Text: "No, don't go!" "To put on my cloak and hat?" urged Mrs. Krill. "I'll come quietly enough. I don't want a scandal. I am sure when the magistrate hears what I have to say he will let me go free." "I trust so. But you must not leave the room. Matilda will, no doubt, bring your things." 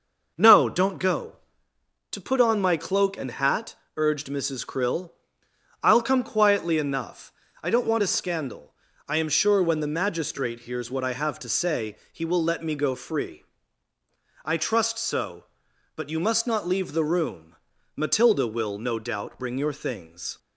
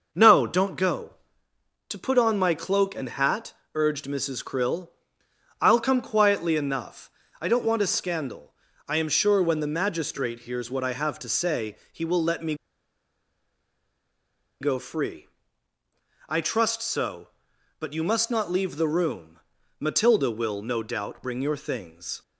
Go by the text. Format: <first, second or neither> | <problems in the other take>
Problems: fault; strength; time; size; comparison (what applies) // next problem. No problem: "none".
first | pauses between "say" and "he"; slight; at 11.7 s; 0.16 s long; slight in the first // pauses between "me" and "go"; strong; at 12.5 s; 2.0 s long